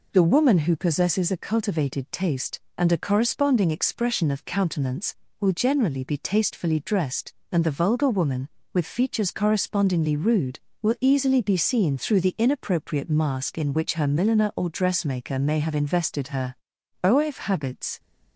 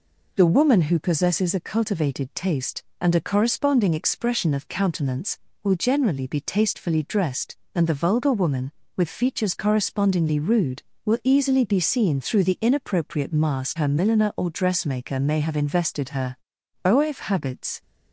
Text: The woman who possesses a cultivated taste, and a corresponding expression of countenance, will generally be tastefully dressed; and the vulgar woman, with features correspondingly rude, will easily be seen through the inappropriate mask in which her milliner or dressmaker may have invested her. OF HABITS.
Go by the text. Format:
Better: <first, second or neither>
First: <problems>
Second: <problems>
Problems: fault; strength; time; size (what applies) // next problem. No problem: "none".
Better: first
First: none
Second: skips "in which"; at 13.7 s